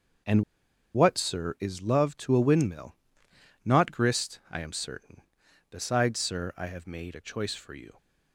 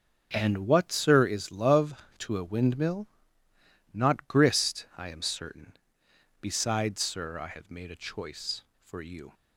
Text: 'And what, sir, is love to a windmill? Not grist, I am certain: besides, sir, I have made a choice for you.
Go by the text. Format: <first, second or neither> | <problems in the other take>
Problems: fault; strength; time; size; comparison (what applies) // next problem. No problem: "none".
second | starts louder than the rest; until 1.8 s; 6.5 dB; also in the second // pauses between "And" and "what"; noticeable; at 0.4 s; 0.51 s long